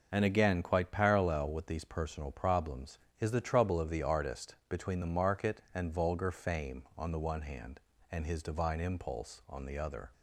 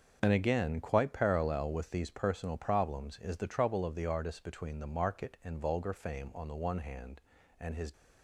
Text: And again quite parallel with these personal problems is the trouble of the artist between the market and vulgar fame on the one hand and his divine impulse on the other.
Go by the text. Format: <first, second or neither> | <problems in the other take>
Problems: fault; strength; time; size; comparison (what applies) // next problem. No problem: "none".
first | starts louder than the rest; until 1.2 s; 6.5 dB // stops before "divine impulse on the other"; at 7.9 s